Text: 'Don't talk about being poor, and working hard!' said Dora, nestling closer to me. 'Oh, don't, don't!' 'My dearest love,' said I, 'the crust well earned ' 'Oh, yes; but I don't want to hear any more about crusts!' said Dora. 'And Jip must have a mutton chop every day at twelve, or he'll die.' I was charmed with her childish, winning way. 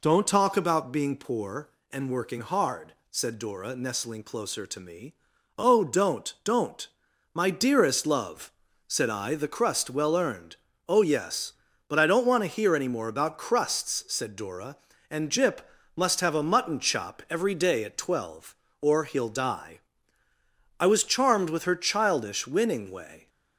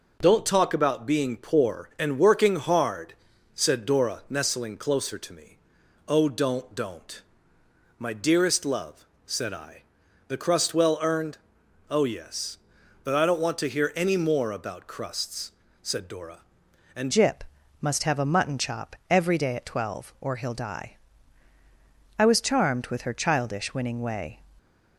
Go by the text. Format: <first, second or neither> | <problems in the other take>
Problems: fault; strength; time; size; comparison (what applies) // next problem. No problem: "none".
first | changes voice at "Jip"; from 17.1 s on; 7.2 s long // pauses between "Jip" and "must"; at 17.4 s; 0.38 s long; slight in the first